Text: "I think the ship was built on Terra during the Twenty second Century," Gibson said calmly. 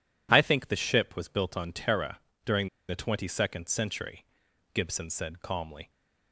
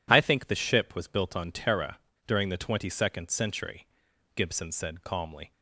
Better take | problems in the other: second | pauses between "Terra" and "during"; slight; at 2.1 s; 0.24 s long; slight in the second // pauses between "during" and "the"; slight; at 2.6 s; 0.20 s long

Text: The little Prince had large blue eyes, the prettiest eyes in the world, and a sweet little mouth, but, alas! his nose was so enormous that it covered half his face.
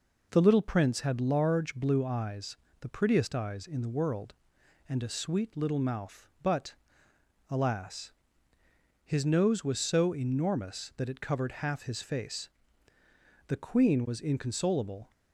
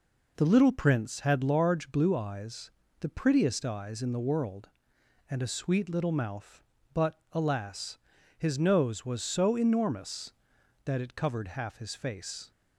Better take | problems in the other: second | goes on to say "The Queen was inconsolable"; from 13.4 s on; 1.6 s long

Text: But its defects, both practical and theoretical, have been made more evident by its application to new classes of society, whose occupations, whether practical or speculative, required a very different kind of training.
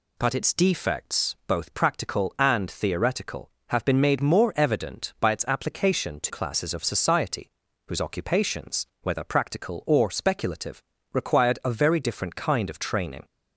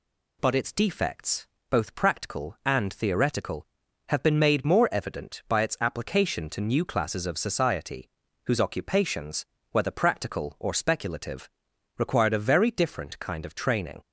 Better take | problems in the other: second | skips "new"; at 6.3 s

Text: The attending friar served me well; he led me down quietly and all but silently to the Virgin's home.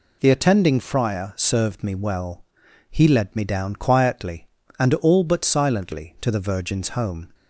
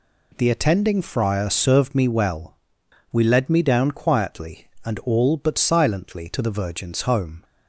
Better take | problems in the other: first | says "we" for "he"; at 3.1 s

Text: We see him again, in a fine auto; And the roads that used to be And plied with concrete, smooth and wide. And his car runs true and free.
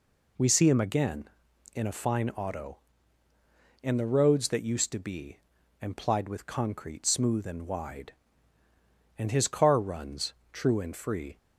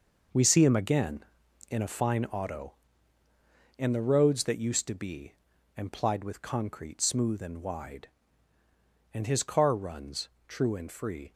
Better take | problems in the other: first | gets quieter; strong; throughout; 8.5 dB // pauses between "runs" and "true"; slight; at 10.2 s; 0.18 s long; slight in the first

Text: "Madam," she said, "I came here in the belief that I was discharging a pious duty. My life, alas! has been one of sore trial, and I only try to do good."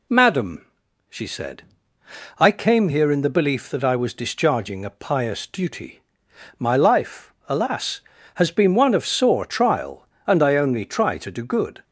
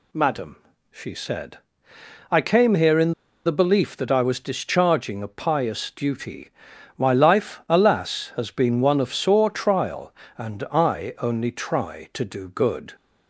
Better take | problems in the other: first | pauses between "in" and "the"; slight; at 3.1 s; 0.34 s long

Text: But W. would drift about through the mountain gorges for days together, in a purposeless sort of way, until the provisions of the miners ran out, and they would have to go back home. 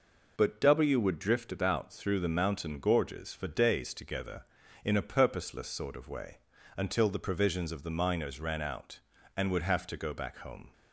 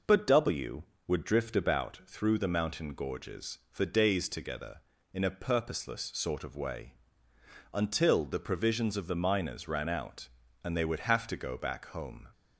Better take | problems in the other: second | skips "they"; at 9.5 s

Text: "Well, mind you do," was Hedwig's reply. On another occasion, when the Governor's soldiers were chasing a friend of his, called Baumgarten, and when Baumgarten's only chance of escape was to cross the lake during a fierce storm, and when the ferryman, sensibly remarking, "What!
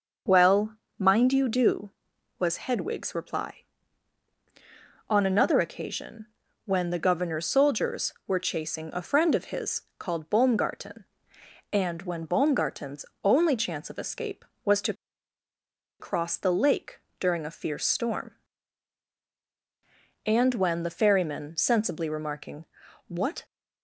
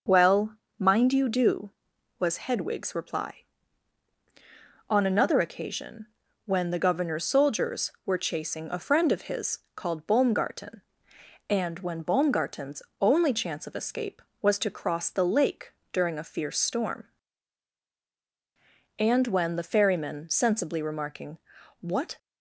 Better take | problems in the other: second | pauses between "Baumgarten's" and "only"; slight; at 13.0 s; 0.18 s long; slight in the second // pauses between "to" and "cross"; at 14.9 s; 1.0 s long // pauses between "lake" and "during"; slight; at 16.9 s; 0.22 s long; slight in the second

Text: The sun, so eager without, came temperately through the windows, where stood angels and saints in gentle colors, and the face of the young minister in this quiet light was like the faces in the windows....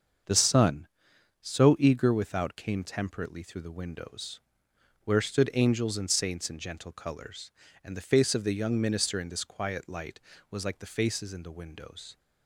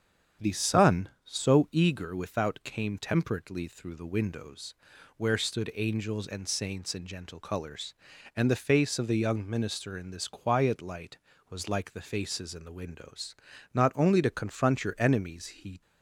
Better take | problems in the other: first | starts louder than the rest; strong; until 1.5 s; 8 dB; also in the first // goes on to say "Not only to confront your enemies he"; strong; from 13.7 s on; 2.0 s long

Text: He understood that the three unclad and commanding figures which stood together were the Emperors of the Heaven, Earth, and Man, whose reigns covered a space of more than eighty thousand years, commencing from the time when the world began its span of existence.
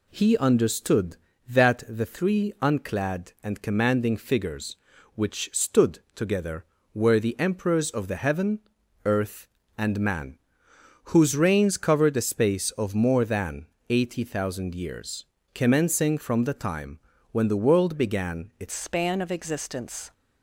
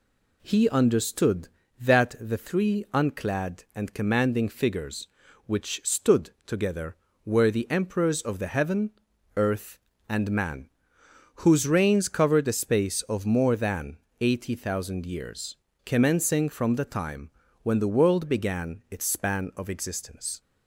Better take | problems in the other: second | pauses between "stood" and "together"; slight; at 5.9 s; 0.16 s long; slight in the second // pauses between "than" and "eighty"; slight; at 13.6 s; 0.22 s long; slight in the second // pauses between "time" and "when"; slight; at 16.9 s; 0.32 s long; slight in the second // changes voice at "span"; from 18.7 s on; 1.4 s long

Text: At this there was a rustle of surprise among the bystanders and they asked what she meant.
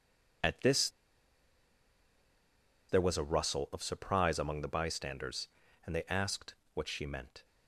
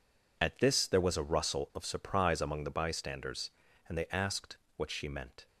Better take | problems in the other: second | pauses between "this" and "there"; strong; at 0.8 s; 2.0 s long // pauses between "asked" and "what"; slight; at 6.5 s; 0.20 s long; slight in the second

